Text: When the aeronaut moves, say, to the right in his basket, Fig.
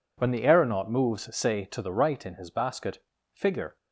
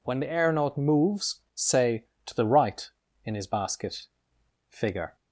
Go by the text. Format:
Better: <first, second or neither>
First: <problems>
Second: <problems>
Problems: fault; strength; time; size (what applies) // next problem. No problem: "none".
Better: neither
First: none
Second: none